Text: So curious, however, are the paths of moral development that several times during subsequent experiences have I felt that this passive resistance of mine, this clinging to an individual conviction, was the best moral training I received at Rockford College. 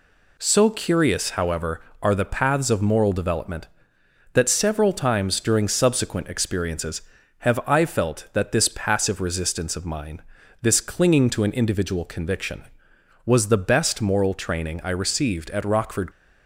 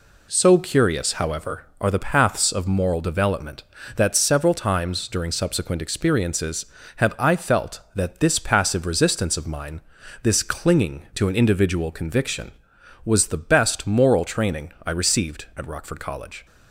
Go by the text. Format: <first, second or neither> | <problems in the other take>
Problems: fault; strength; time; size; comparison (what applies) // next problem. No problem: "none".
second | stops before "College"; at 16.1 s